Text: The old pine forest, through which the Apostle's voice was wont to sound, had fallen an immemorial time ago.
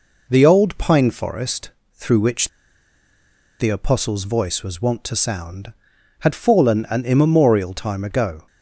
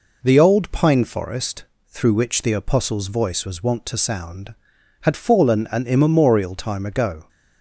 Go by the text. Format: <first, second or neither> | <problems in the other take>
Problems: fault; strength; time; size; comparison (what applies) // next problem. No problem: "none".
second | pauses between "which" and "the"; at 2.4 s; 1.1 s long